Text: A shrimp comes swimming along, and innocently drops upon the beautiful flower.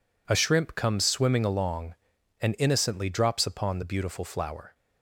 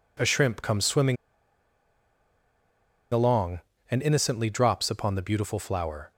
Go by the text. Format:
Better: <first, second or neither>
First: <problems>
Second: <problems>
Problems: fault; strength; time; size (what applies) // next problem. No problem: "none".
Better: first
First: none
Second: pauses between "swimming" and "along"; strong; at 1.1 s; 1.9 s long